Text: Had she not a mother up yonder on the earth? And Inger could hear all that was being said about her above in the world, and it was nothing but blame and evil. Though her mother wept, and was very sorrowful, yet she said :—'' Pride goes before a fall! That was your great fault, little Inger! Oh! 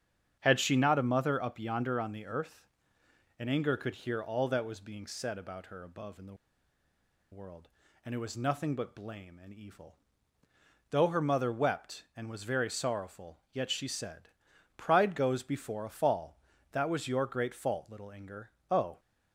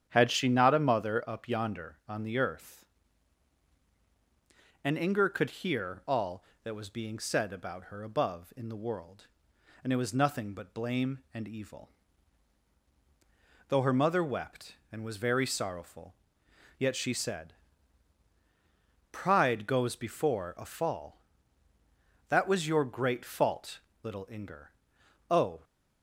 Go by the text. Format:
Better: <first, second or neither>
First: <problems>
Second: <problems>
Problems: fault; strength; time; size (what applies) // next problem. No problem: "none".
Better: second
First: starts louder than the rest; strong; until 1.4 s; 8 dB // pauses between "the" and "world"; noticeable; at 6.3 s; 0.97 s long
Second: starts louder than the rest; strong; until 1.1 s; 8.5 dB